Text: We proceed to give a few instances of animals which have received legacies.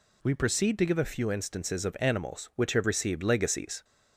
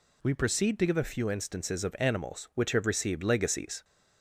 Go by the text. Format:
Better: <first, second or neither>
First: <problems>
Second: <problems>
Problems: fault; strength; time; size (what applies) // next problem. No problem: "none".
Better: neither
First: none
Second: none